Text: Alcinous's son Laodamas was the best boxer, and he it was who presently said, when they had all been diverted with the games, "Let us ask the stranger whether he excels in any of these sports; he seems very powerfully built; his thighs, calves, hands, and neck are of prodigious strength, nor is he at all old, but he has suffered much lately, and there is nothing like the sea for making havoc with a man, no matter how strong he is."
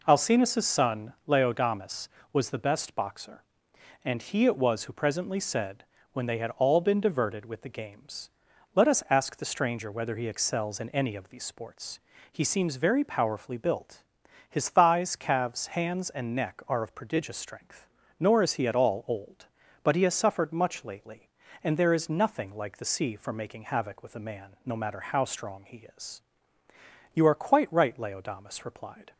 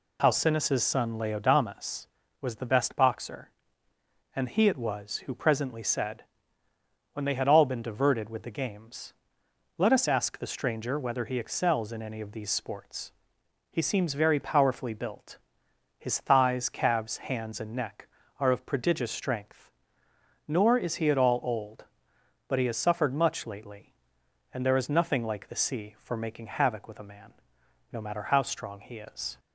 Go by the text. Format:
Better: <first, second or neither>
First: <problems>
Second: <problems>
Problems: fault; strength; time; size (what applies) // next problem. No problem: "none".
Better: second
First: pauses between "son" and "Laodamas"; slight; at 1.1 s; 0.16 s long // goes on to say "You are quite right Laodamas replied"; strong; from 27.1 s on; 1.9 s long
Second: none